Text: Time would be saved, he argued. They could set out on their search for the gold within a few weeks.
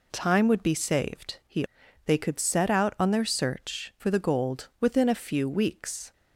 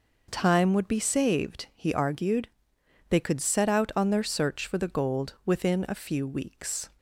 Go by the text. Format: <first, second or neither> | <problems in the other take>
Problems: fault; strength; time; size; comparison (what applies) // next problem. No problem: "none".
second | skips "argued"; at 1.8 s